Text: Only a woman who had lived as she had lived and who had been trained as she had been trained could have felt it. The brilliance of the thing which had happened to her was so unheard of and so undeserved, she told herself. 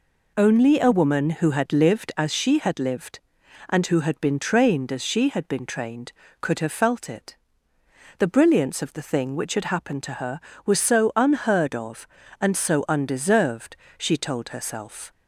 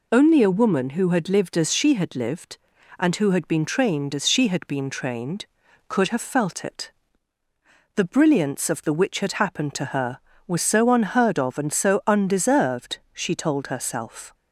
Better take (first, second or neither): first